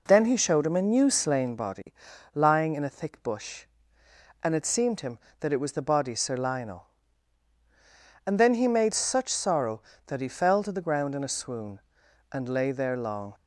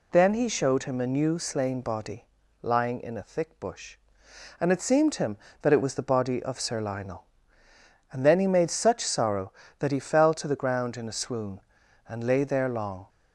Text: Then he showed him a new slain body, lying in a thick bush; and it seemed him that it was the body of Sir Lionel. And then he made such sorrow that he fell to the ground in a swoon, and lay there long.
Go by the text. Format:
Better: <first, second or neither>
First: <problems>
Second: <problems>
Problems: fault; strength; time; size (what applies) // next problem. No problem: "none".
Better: second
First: skips "of"; at 6.1 s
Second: none